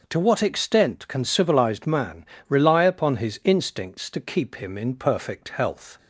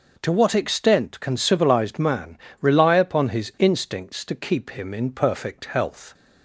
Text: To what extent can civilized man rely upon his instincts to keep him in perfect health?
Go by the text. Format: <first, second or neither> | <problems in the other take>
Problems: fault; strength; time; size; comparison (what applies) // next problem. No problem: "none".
neither | pauses between "man" and "rely"; slight; the same in both